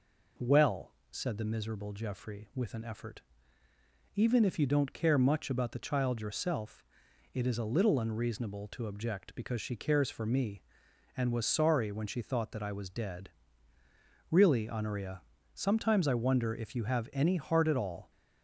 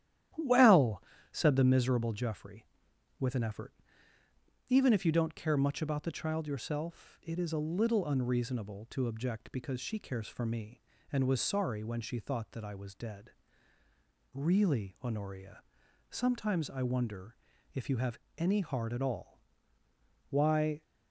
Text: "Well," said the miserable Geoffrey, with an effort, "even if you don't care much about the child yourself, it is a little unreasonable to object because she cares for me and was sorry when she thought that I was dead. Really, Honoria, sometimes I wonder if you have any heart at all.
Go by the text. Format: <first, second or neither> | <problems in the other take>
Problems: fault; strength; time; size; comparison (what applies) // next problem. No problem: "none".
first | starts louder than the rest; strong; until 1.6 s; 11.5 dB // pauses between "wonder" and "if"; at 17.3 s; 0.40 s long // pauses between "have" and "any"; slight; at 18.2 s; 0.18 s long // goes on to say "Why"; from 20.2 s on; 0.54 s long